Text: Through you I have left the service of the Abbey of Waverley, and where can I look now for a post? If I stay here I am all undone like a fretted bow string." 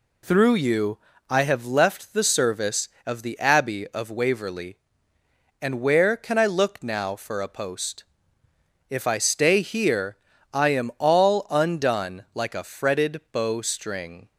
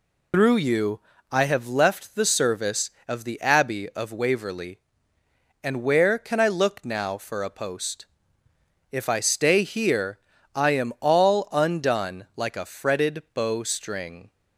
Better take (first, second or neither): first